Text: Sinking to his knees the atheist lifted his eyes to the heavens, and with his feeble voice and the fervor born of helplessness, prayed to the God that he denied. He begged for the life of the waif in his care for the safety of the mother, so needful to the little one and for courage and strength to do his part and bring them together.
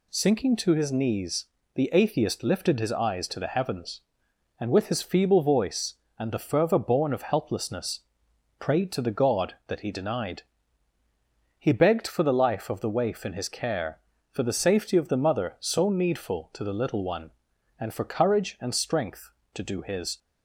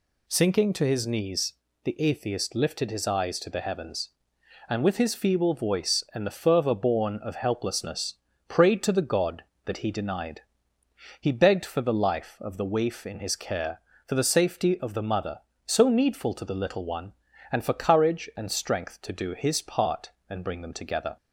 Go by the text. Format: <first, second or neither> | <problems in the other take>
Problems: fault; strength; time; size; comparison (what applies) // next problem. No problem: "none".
second | pauses between "knees" and "the"; slight; at 1.4 s; 0.30 s long; slight in the second // stops before "part and bring them together"; at 20.1 s